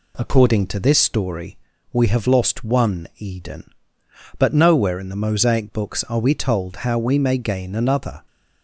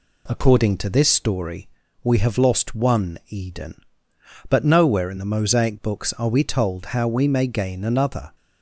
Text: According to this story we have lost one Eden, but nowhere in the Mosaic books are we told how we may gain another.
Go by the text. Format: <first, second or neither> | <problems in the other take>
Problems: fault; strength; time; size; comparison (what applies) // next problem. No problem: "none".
neither | pauses between "story" and "we"; slight; the same in both